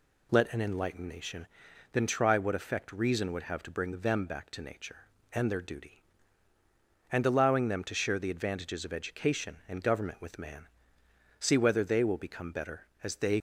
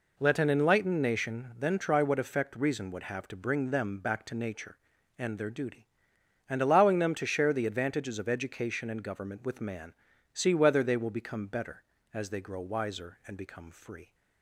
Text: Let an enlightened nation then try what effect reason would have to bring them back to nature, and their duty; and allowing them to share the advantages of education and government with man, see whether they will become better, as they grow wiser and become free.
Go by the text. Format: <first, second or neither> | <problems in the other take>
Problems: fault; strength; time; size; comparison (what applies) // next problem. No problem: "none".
second | pauses between "nation" and "then"; noticeable; at 1.4 s; 0.46 s long // stops before "grow wiser and become free"; at 13.3 s